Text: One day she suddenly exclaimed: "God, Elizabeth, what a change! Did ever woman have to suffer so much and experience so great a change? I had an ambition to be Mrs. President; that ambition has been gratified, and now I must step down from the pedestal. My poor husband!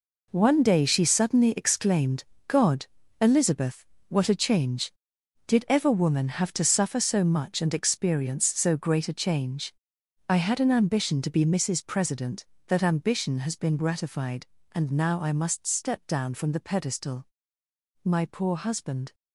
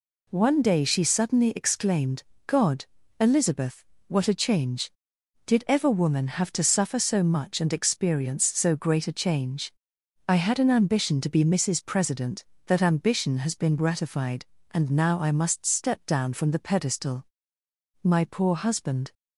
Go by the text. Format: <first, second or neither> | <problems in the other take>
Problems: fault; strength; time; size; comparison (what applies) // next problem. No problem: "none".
second | gets quieter; strong; throughout; 10.5 dB